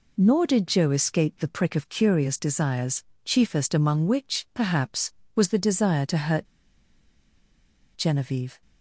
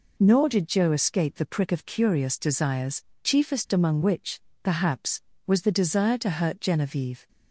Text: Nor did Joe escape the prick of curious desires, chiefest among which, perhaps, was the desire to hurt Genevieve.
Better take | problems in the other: second | pauses between "hurt" and "Genevieve"; strong; at 6.4 s; 1.5 s long

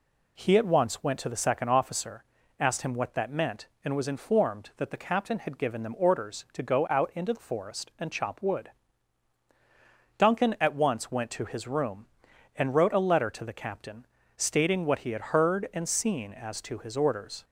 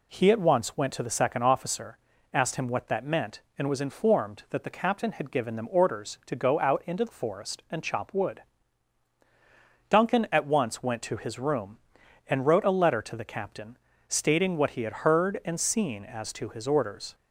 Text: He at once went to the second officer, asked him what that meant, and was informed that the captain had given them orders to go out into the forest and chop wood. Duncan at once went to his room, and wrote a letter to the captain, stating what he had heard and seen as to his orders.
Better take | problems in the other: neither | none

